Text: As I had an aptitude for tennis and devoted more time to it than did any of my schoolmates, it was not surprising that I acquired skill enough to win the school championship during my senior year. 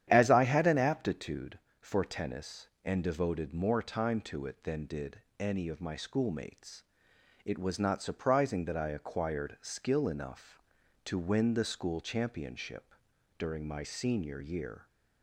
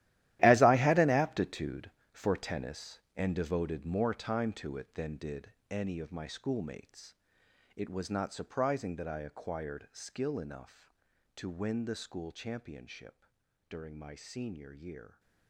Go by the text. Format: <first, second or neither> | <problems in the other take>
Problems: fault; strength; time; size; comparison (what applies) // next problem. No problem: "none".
first | gets quieter; strong; throughout; 14 dB // starts louder than the rest; strong; until 1.4 s; 14 dB; strong in the first // pauses between "did" and "any"; slight; at 5.5 s; 0.18 s long; slight in the first // pauses between "championship" and "during"; at 13.2 s; 0.42 s long; also in the first